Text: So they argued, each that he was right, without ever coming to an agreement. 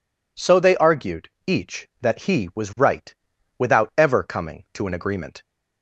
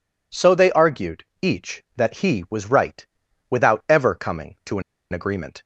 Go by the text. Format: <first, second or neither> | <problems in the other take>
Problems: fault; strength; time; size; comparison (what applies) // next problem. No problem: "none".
first | pauses between "an" and "agreement"; slight; at 4.8 s; 0.30 s long